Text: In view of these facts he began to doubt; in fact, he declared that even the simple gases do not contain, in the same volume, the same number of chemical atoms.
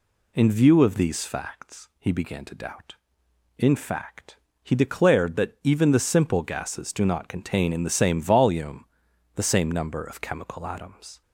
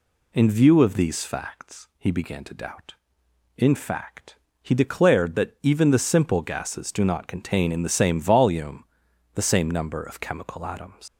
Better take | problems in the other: first | leaves "atoms" unfinished; at 11.0 s; 125 ms

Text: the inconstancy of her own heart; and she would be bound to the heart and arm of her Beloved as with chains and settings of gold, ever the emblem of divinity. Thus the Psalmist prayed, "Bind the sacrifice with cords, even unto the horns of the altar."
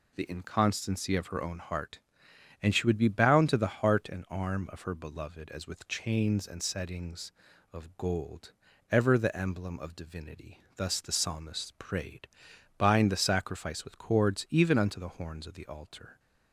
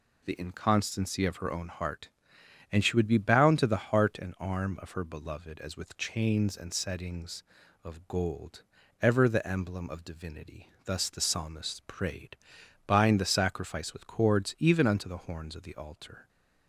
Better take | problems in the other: neither | none

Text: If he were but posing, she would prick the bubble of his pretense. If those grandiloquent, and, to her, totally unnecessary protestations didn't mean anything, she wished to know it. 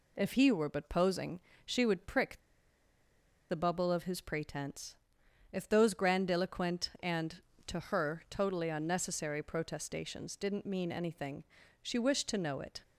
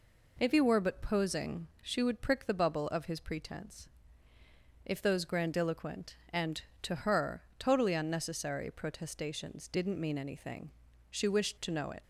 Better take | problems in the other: second | pauses between "prick" and "the"; at 2.3 s; 1.1 s long

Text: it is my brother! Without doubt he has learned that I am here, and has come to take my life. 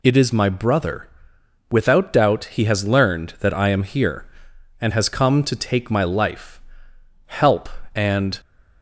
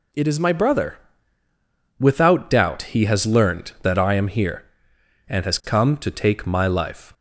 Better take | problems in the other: second | goes on to say "Help and"; noticeable; from 7.2 s on; 1.1 s long

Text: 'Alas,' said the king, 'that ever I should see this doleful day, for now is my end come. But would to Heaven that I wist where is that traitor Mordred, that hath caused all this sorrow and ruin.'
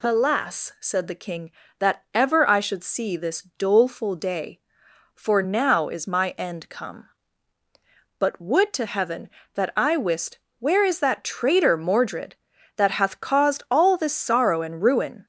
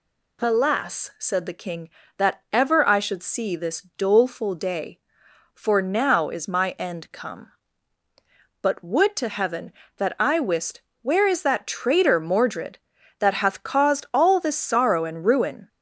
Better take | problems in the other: neither | pauses between "this" and "doleful"; slight; the same in both // pauses between "wist" and "where"; slight; the same in both

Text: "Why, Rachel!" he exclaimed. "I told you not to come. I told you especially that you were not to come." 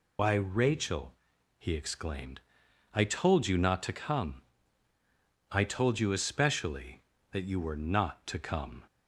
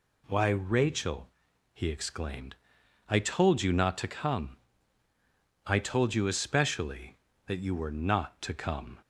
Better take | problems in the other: second | loses the start of "Why"; at 0.1 s; 105 ms

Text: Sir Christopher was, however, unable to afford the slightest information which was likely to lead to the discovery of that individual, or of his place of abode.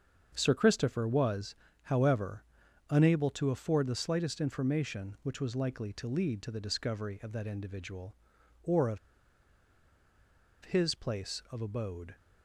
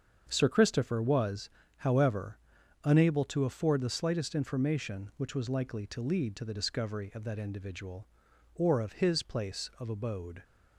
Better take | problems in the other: second | starts louder than the rest; until 1.3 s; 7 dB; also in the second // pauses between "of" and "his"; strong; at 8.9 s; 1.6 s long

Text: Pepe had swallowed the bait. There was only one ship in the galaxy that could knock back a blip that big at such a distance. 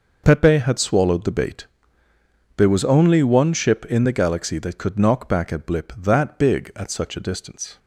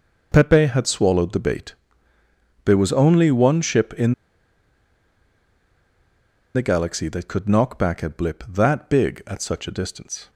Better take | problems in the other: first | pauses between "in" and "the"; strong; at 4.1 s; 2.4 s long

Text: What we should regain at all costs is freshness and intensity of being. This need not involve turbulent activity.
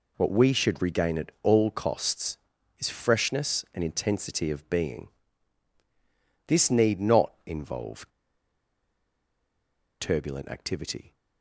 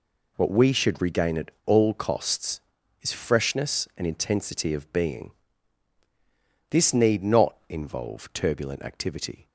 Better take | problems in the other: second | pauses between "involve" and "turbulent"; strong; at 8.0 s; 1.9 s long

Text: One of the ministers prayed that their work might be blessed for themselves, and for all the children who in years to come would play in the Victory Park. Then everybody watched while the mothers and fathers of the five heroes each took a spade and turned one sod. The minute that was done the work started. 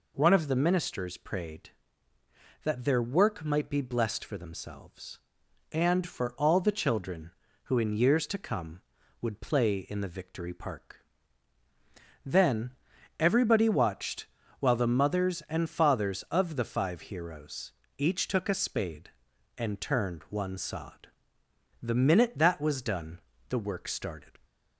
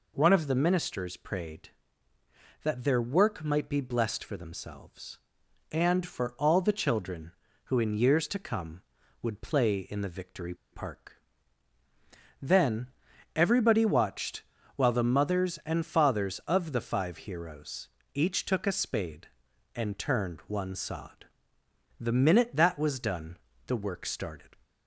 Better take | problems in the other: first | pauses between "Victory" and "Park"; slight; at 10.5 s; 0.17 s long // pauses between "Then" and "everybody"; at 12.9 s; 0.44 s long; also in the first // pauses between "watched" and "while"; slight; at 14.4 s; 0.34 s long; slight in the first // pauses between "heroes" and "each"; slight; at 17.8 s; 0.26 s long; slight in the first // pauses between "done" and "the"; slight; at 23.3 s; 0.30 s long; slight in the first

